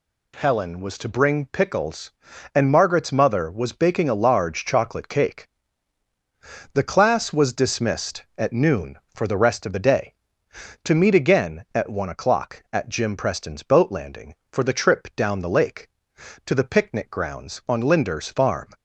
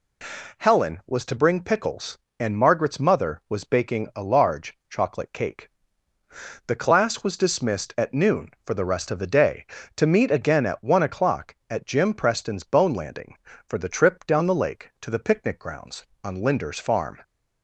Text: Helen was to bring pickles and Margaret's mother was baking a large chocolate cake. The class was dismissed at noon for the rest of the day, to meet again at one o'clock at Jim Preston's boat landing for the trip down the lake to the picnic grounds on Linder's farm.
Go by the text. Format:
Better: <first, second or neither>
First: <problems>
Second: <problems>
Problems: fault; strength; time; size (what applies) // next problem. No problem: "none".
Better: first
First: none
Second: says "bone" for "boat"; at 12.6 s